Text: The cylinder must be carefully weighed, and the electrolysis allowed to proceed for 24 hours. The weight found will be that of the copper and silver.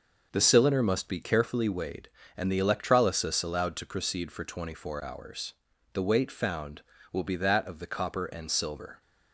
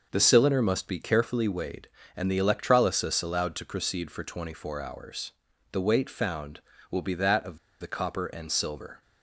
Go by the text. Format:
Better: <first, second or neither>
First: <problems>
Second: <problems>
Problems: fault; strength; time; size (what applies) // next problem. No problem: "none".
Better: first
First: none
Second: pauses between "of" and "the"; slight; at 7.5 s; 0.22 s long